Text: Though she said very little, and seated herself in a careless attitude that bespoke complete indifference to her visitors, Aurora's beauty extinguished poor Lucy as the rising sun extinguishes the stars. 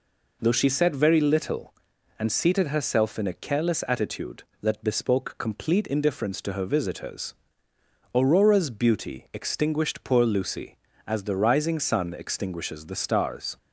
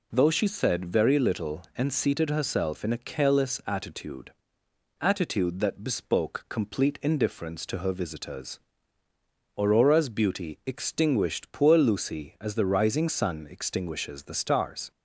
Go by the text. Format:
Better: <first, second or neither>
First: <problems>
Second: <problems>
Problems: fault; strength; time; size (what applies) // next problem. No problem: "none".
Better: first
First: none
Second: says "attitude" twice; at 4.9 s